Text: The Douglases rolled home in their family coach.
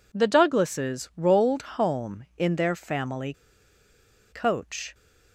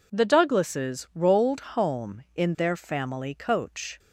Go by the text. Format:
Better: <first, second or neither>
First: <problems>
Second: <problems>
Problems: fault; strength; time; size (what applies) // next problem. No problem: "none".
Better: second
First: pauses between "family" and "coach"; at 3.3 s; 0.99 s long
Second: none